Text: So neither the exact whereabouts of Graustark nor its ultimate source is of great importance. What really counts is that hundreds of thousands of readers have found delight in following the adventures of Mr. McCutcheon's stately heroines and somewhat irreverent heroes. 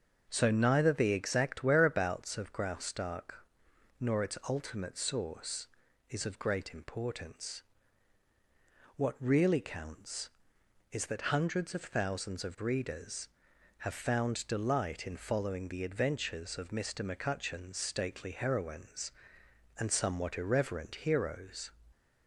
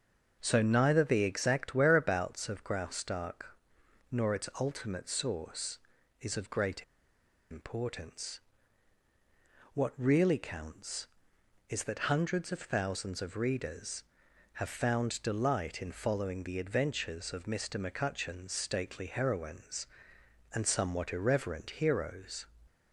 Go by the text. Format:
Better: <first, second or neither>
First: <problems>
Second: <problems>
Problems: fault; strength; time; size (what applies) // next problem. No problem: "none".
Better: first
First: starts louder than the rest; until 1.3 s; 6.5 dB // pauses between "Graustark" and "nor"; noticeable; at 3.4 s; 0.56 s long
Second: starts louder than the rest; until 1.4 s; 6.5 dB // pauses between "Graustark" and "nor"; noticeable; at 3.5 s; 0.56 s long // pauses between "great" and "importance"; noticeable; at 6.8 s; 0.67 s long